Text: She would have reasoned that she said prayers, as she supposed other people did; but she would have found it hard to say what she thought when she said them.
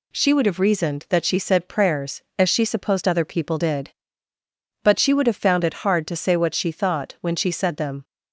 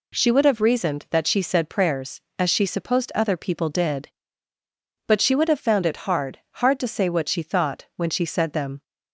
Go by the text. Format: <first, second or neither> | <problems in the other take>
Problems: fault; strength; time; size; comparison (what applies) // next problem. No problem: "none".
first | says "hard" twice; at 6.5 s